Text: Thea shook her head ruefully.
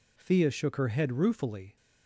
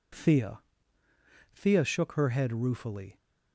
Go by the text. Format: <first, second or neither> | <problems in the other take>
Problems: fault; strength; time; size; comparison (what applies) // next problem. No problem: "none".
first | says "Thea" twice; at 1.5 s